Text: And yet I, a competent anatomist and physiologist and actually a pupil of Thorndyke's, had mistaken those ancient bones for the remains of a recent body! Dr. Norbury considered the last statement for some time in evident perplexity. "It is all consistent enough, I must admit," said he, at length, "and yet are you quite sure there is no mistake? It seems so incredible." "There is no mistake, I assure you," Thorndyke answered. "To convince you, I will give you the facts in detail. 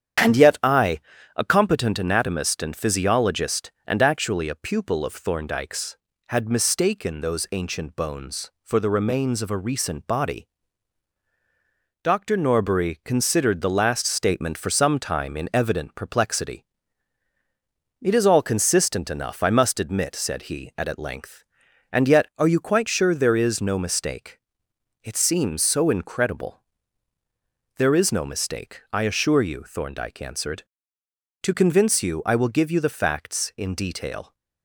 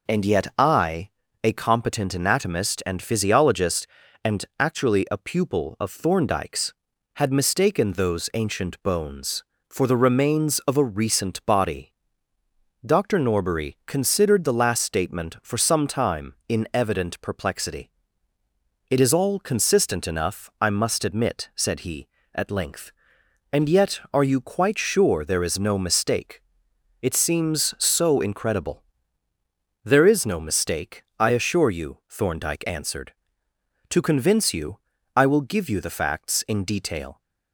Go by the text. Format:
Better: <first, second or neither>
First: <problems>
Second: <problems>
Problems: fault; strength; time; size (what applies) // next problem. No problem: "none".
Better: second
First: starts louder than the rest; strong; until 1.6 s; 8.5 dB // says "at" twice; at 20.8 s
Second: none